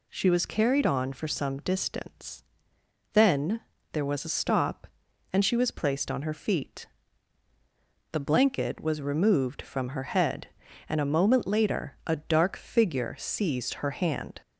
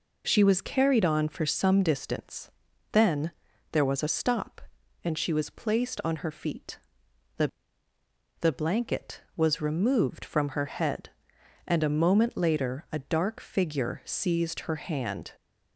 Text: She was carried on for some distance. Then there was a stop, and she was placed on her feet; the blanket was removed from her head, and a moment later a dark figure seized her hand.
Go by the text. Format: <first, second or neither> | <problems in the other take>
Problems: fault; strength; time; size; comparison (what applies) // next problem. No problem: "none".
first | pauses between "Then" and "there"; at 3.3 s; 0.40 s long; slight in the first // says "the" twice; at 8.3 s